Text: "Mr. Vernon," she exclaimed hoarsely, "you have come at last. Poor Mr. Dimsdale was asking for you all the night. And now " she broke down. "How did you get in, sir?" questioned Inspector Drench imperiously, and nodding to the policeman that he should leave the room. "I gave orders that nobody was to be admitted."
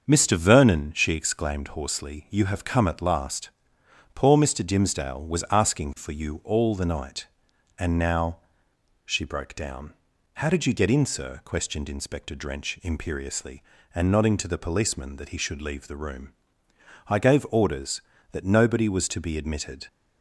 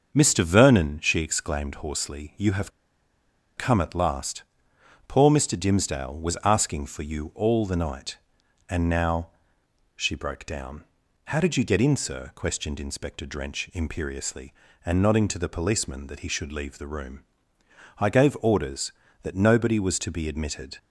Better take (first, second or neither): first